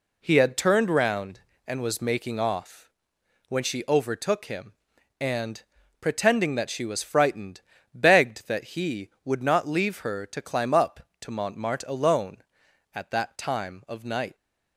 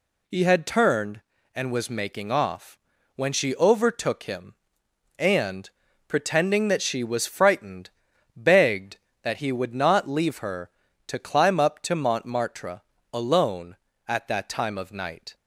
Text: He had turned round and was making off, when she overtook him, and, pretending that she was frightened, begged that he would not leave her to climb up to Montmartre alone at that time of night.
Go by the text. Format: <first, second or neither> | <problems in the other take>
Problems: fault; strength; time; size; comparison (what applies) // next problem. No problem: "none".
first | skips "round"; at 1.3 s // pauses between "Montmartre" and "alone"; slight; at 12.8 s; 0.30 s long